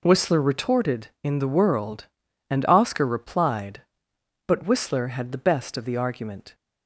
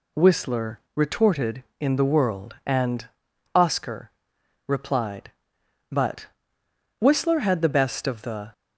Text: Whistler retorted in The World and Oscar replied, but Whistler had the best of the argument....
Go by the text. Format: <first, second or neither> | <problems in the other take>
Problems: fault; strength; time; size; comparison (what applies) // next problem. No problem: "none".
first | pauses between "Whistler" and "retorted"; slight; at 0.7 s; 0.16 s long // pauses between "and" and "Oscar"; noticeable; at 3.0 s; 0.48 s long // pauses between "Oscar" and "replied"; noticeable; at 4.1 s; 0.56 s long // pauses between "but" and "Whistler"; noticeable; at 6.2 s; 0.72 s long // stops before "argument"; at 8.5 s